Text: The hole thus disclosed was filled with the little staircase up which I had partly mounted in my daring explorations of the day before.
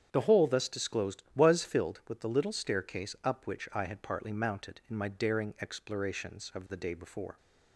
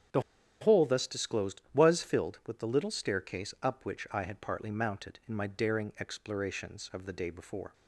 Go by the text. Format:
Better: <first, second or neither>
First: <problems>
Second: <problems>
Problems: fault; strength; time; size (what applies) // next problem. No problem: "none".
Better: first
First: starts louder than the rest; strong; until 1.1 s; 8.5 dB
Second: starts louder than the rest; strong; until 1.5 s; 8.5 dB // pauses between "The" and "hole"; at 0.2 s; 0.40 s long